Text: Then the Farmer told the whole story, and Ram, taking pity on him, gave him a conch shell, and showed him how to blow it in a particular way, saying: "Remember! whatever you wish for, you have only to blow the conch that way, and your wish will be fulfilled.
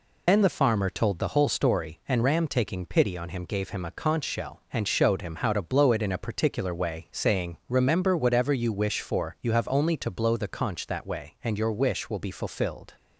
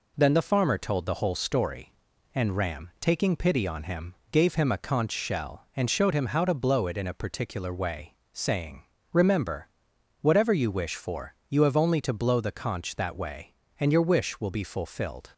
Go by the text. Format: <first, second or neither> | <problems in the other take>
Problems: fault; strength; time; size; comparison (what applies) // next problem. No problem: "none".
second | loses the start of "Then"; at 0.2 s; 95 ms